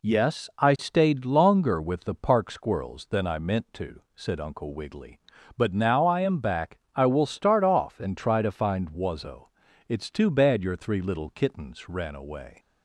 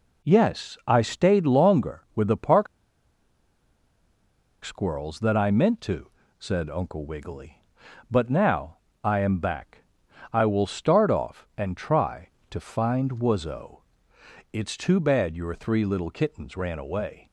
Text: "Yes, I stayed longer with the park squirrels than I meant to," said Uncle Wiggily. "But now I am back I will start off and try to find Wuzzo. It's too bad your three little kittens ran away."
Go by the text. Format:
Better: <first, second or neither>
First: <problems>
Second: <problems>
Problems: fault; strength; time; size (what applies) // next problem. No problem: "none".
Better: first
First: pauses between "back" and "I"; slight; at 6.7 s; 0.16 s long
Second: pauses between "park" and "squirrels"; strong; at 2.6 s; 1.9 s long // pauses between "now" and "I"; slight; at 8.7 s; 0.26 s long // pauses between "back" and "I"; noticeable; at 9.8 s; 0.50 s long